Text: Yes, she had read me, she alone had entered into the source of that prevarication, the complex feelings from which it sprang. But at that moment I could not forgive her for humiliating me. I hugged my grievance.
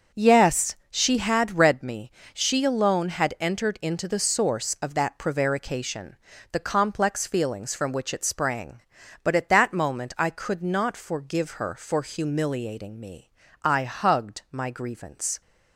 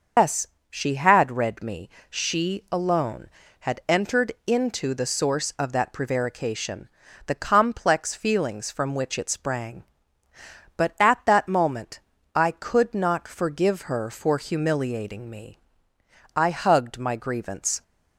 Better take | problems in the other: first | loses the start of "Yes"; at 0.1 s; 145 ms // starts louder than the rest; noticeable; until 1.4 s; 6 dB; also in the first // pauses between "moment" and "I"; slight; at 11.9 s; 0.36 s long

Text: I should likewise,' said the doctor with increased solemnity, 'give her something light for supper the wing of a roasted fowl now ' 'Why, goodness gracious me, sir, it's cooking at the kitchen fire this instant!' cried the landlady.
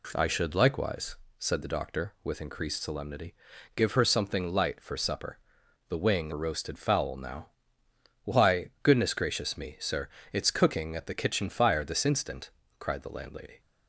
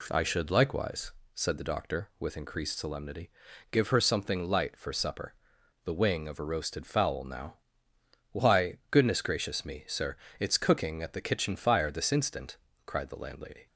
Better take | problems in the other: second | pauses between "supper" and "the"; noticeable; at 5.3 s; 0.48 s long; noticeable in the second // skips "of"; at 6.3 s

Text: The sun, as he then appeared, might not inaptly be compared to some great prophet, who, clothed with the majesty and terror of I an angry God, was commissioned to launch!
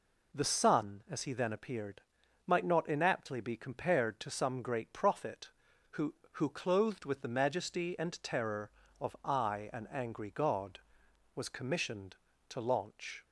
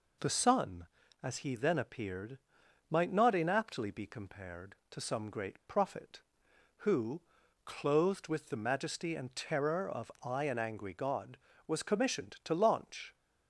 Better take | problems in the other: second | says "who" twice; at 6.3 s

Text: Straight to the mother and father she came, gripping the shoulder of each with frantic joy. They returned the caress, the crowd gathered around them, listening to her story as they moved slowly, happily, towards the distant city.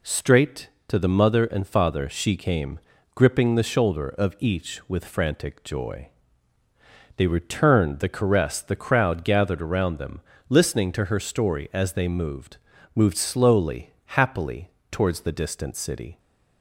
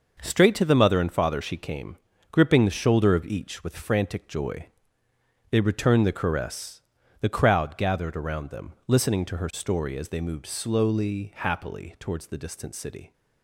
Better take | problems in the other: second | says "moved" twice; at 12.9 s

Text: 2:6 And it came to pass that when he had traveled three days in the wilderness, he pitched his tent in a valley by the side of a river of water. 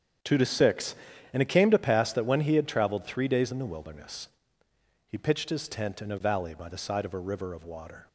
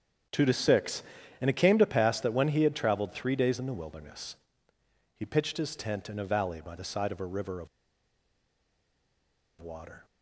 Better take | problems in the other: first | starts louder than the rest; strong; until 1.6 s; 8.5 dB; strong in the first // pauses between "of" and "water"; strong; at 7.6 s; 1.9 s long

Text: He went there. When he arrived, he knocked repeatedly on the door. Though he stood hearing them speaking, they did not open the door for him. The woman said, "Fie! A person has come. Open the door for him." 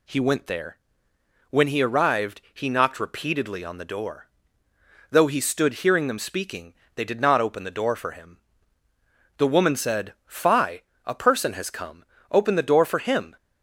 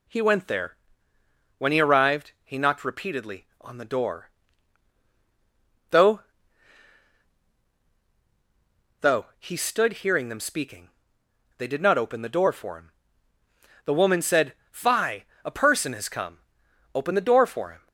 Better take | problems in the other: first | says "Though" twice; at 9.0 s

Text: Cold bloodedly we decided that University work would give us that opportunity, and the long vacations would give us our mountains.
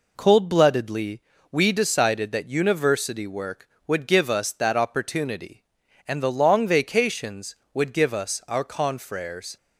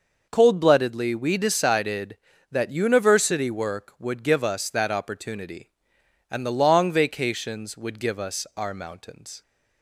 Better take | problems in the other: second | pauses between "bloodedly" and "we"; slight; at 1.2 s; 0.32 s long // says "confreres" for "mountains"; at 8.6 s

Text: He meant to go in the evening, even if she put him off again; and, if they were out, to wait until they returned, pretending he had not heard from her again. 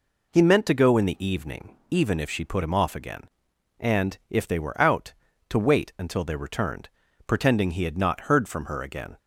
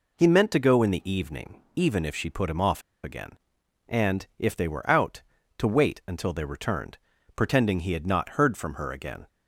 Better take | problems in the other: first | pauses between "off" and "again"; slight; at 2.8 s; 0.22 s long

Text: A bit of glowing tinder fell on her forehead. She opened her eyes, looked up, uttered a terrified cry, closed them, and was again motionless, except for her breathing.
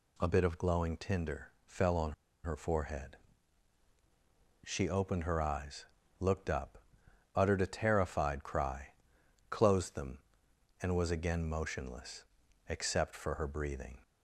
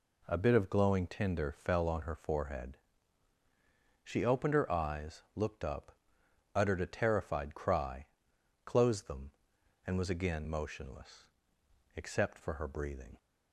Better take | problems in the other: second | pauses between "tinder" and "fell"; slight; at 1.4 s; 0.18 s long // pauses between "on" and "her"; slight; at 2.1 s; 0.30 s long

